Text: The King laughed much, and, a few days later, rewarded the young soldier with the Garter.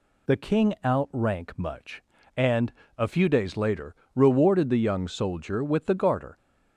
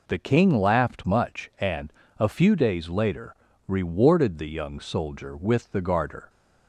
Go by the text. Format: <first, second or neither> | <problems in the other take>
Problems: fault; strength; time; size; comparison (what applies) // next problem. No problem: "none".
second | says "outrank" for "laughed"; at 0.8 s